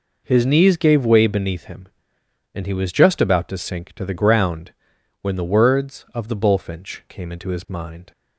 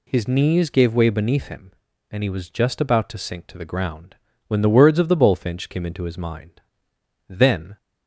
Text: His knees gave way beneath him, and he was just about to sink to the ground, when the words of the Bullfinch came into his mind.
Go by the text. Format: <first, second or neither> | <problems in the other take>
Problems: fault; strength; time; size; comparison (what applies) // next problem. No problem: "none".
first | goes on to say "Then"; slight; from 7.2 s on; 0.48 s long